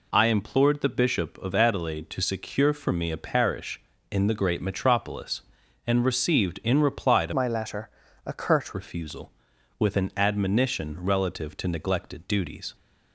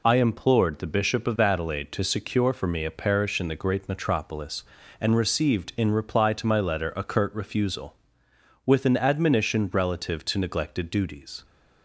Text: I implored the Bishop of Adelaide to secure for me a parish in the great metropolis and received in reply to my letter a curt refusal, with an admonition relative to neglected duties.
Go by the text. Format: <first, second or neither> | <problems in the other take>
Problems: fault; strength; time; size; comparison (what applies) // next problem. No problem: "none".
second | changes voice from "my" to "curt"; from 7.3 to 8.7 s; 1.4 s long // pauses between "letter" and "a"; slight; at 7.8 s; 0.36 s long